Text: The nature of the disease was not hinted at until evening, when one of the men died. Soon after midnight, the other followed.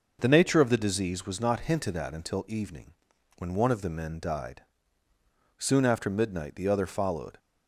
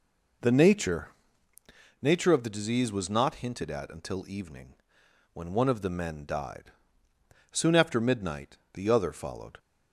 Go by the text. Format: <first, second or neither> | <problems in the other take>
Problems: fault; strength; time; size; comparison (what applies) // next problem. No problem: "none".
first | says "nature" twice; at 1.9 s